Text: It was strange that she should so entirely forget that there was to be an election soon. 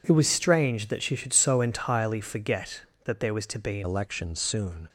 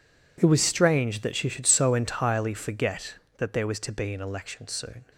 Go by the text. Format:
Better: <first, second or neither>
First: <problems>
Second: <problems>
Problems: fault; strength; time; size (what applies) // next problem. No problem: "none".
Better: second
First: changes voice at "election"; from 3.8 s on; 1.0 s long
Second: none